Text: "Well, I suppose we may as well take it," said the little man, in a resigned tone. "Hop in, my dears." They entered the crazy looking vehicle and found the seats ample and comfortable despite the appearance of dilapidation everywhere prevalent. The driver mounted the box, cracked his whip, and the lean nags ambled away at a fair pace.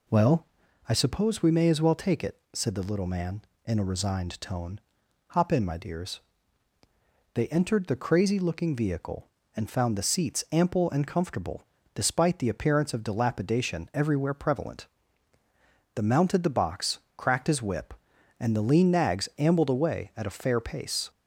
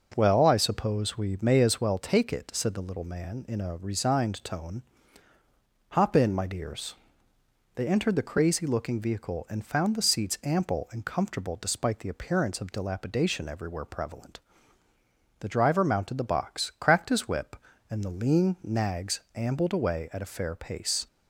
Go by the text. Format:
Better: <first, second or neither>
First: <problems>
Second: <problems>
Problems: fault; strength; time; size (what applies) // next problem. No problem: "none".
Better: second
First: pauses between "comfortable" and "despite"; slight; at 11.6 s; 0.30 s long // skips "driver"; at 16.0 s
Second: none